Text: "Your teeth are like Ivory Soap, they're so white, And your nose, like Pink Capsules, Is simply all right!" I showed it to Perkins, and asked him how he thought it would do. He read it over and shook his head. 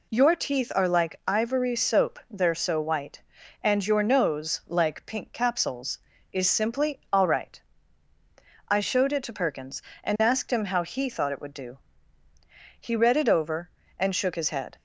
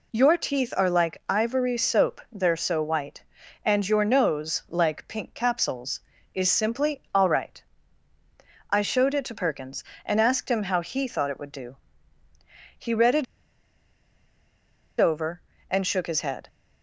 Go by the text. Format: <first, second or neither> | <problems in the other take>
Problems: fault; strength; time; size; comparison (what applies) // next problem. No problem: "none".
first | pauses between "it" and "over"; strong; at 13.2 s; 1.7 s long